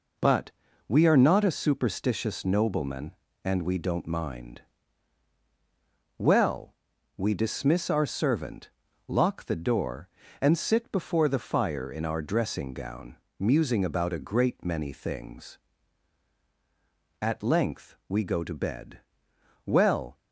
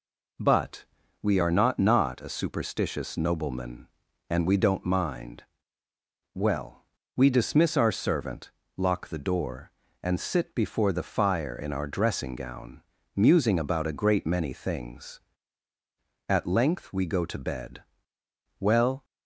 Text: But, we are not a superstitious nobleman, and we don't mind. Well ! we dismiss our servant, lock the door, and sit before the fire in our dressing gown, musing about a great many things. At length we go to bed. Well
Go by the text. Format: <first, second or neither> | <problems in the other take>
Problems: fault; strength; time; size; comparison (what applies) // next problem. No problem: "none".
first | says "not" twice; at 1.7 s